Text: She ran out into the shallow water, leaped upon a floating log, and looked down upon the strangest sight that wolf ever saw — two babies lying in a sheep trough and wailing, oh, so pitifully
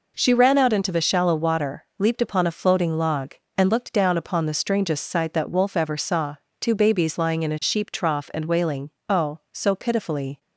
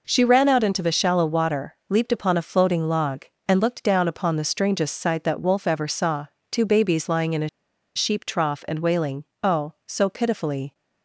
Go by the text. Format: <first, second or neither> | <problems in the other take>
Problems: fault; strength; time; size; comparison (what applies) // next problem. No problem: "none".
first | pauses between "a" and "sheep"; noticeable; at 7.4 s; 0.48 s long